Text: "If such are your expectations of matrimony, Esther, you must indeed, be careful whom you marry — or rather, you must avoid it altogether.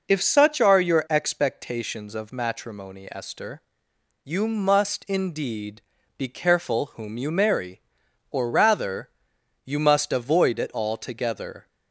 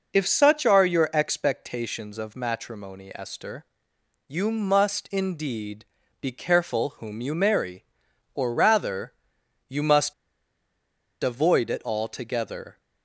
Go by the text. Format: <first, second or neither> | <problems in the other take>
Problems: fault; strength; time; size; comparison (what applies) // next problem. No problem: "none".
first | pauses between "must" and "avoid"; at 10.1 s; 1.0 s long